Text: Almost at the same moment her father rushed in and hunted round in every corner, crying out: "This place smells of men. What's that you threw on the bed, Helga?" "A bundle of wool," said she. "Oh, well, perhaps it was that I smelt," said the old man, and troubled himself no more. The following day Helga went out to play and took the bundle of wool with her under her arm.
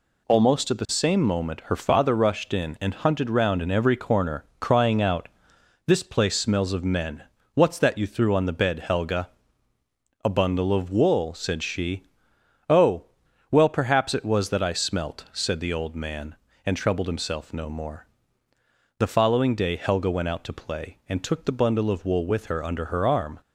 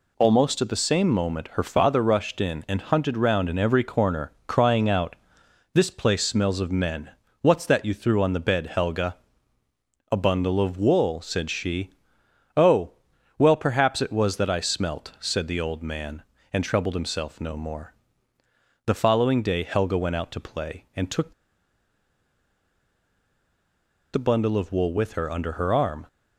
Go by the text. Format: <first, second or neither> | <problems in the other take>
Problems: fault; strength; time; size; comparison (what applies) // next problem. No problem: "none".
first | pauses between "took" and "the"; strong; at 21.3 s; 2.8 s long